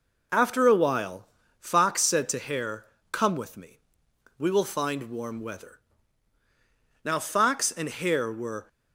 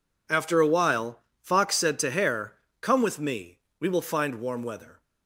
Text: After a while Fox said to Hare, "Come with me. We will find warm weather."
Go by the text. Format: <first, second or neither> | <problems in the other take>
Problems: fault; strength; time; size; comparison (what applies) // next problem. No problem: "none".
second | pauses between "while" and "Fox"; slight; at 1.2 s; 0.32 s long; slight in the second // goes on to say "Now Fox and Hare were"; from 7.0 s on; 1.6 s long